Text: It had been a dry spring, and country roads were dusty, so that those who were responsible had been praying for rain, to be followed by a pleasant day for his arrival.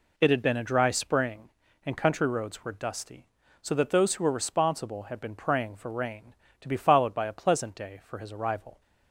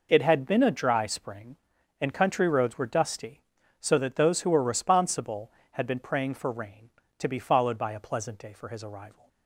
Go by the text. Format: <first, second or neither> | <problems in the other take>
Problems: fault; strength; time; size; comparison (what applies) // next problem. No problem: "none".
neither | none